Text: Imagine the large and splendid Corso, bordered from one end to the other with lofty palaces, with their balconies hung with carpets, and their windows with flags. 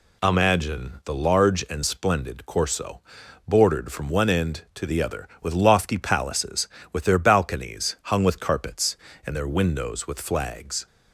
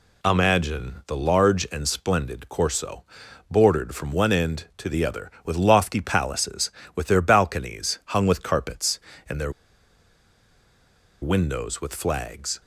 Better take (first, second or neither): first